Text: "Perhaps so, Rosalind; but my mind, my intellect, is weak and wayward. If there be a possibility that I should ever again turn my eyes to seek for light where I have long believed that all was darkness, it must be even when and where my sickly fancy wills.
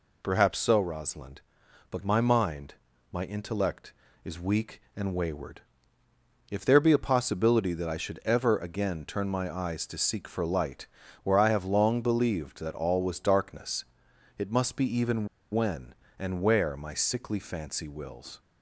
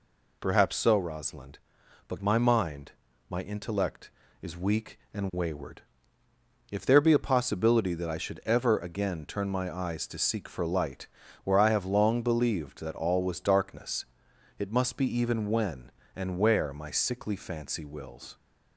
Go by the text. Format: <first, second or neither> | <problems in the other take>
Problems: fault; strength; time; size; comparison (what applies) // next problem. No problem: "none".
second | pauses between "light" and "where"; at 10.8 s; 0.38 s long; also in the second // pauses between "even" and "when"; slight; at 15.2 s; 0.24 s long